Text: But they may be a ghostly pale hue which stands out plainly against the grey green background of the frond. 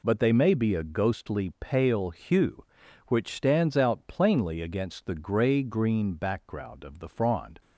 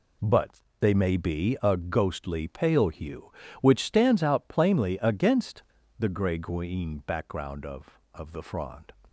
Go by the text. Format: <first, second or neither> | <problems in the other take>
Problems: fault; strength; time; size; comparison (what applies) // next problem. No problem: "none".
first | pauses between "But" and "they"; slight; at 0.6 s; 0.20 s long // pauses between "against" and "the"; slight; at 5.6 s; 0.36 s long // says "of" twice; at 8.1 s